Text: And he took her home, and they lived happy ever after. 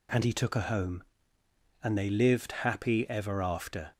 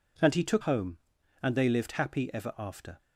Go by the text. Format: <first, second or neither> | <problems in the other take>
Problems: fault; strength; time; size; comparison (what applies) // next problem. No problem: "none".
first | skips "her"; at 0.6 s